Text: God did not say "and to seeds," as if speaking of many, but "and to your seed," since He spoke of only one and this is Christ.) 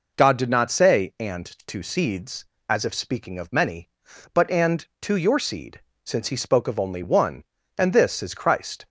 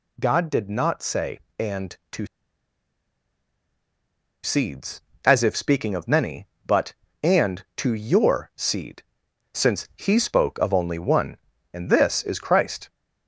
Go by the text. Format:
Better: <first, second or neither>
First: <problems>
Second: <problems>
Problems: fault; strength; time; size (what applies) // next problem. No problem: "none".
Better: first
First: none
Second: pauses between "to" and "seeds"; strong; at 2.2 s; 2.1 s long